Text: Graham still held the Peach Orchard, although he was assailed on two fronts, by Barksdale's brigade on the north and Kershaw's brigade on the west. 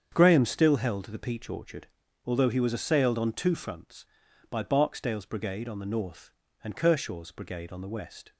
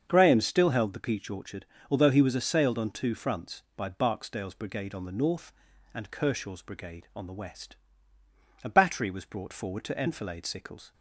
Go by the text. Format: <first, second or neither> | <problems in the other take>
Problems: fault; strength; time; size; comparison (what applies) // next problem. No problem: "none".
first | starts louder than the rest; until 1.0 s; 7 dB; strong in the first // goes on to say "A battery was brought forward to enfilade Sickles"; strong; from 8.6 s on; 2.3 s long